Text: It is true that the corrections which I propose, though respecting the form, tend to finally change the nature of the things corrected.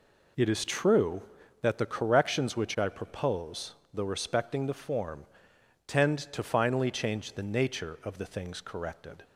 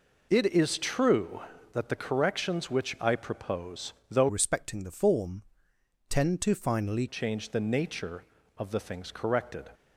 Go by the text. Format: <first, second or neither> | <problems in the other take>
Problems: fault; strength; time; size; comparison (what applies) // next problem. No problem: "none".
first | changes voice from "respecting" to "finally"; from 4.2 to 7.0 s; 2.8 s long